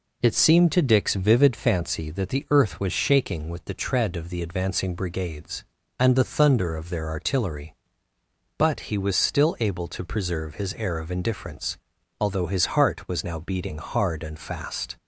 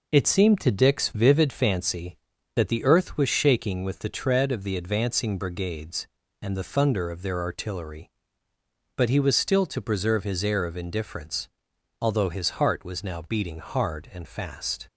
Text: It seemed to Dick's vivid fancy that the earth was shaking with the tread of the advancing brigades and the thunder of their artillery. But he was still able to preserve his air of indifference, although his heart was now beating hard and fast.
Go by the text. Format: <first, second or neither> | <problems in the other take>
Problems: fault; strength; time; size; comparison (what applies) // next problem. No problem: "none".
first | skips "able"; at 9.6 s